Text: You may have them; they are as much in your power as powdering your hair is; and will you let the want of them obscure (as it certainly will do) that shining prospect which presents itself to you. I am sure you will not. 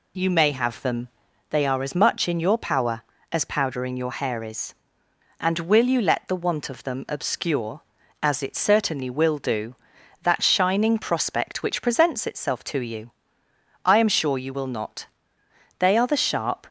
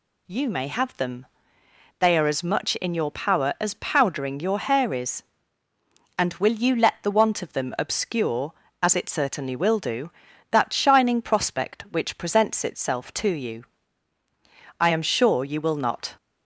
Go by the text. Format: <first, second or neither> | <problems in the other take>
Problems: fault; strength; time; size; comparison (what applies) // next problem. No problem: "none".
second | goes on to say "They are the sharp"; noticeable; from 15.7 s on; 0.88 s long